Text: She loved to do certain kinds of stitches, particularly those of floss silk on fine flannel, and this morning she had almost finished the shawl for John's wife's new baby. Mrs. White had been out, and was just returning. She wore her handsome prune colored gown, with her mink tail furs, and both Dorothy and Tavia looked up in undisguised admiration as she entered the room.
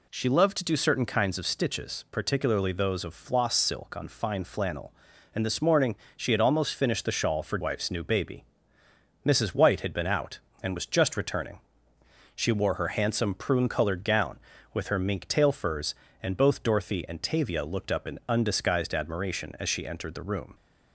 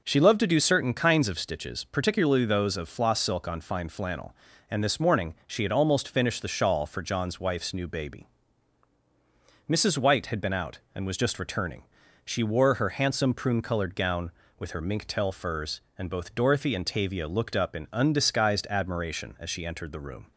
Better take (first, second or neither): second